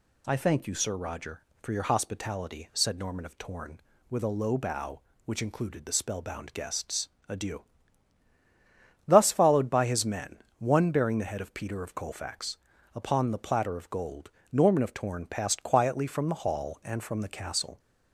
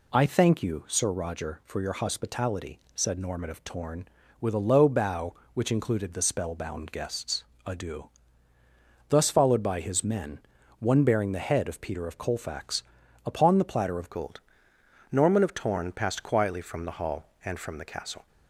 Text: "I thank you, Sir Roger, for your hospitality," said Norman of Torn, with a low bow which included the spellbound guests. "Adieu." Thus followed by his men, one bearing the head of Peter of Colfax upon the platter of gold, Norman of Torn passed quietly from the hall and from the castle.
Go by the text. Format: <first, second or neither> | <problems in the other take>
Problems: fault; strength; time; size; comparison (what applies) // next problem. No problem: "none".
first | pauses between "Colfax" and "upon"; at 12.8 s; 0.42 s long; also in the first // changes voice at "gold"; from 14.1 s on; 4.1 s long